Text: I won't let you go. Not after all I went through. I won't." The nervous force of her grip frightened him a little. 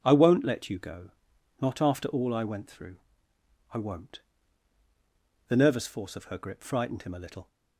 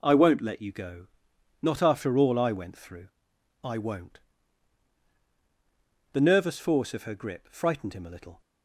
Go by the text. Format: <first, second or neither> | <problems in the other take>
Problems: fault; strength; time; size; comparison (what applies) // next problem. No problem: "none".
neither | none